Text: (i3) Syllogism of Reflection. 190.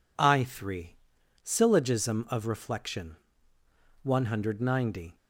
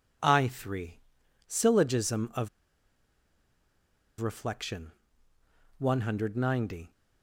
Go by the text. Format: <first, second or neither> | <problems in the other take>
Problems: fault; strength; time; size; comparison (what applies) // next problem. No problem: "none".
first | pauses between "of" and "Reflection"; strong; at 2.4 s; 1.7 s long